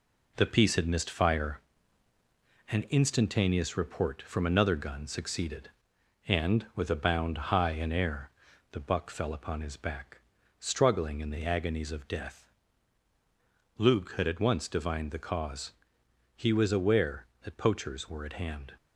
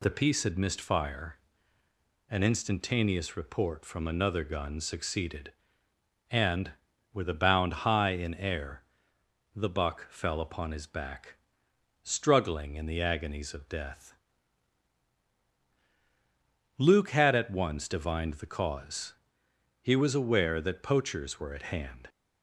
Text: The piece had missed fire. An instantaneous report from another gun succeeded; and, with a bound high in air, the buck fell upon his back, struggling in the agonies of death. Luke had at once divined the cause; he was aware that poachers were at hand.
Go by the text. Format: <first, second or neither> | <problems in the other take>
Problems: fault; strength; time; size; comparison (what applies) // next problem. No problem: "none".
second | gets quieter; noticeable; throughout; 6 dB // pauses between "bound" and "high"; slight; at 7.3 s; 0.16 s long